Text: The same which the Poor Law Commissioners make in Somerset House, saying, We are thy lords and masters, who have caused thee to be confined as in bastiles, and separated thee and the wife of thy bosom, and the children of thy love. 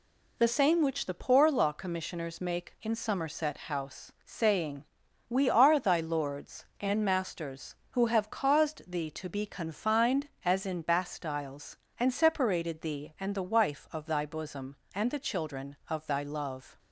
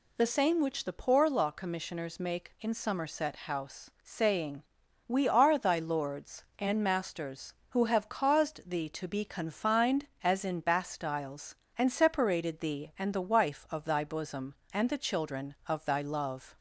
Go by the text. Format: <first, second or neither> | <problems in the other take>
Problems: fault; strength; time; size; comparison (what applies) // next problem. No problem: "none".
second | gets quieter; noticeable; throughout; 4.5 dB